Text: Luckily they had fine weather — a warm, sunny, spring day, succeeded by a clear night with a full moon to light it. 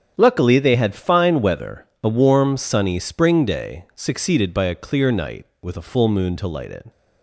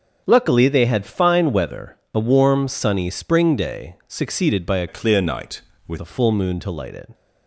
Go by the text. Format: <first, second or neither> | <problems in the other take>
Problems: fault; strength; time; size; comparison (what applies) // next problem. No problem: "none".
first | starts louder than the rest; until 1.2 s; 7 dB; strong in the first // changes voice from "clear" to "with"; from 4.8 to 5.9 s; 1.1 s long